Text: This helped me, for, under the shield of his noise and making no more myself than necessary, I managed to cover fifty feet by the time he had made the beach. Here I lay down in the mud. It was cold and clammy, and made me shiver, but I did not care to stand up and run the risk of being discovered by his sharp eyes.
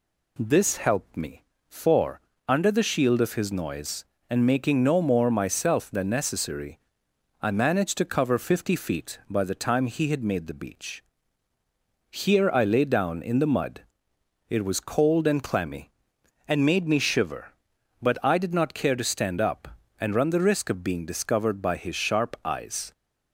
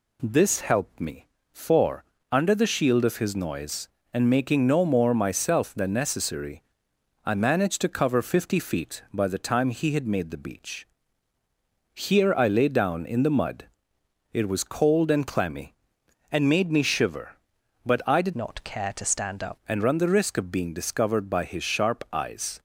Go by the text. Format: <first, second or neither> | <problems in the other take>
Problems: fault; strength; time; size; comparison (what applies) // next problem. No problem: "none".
first | changes voice from "not" to "up"; from 18.3 to 19.5 s; 1.2 s long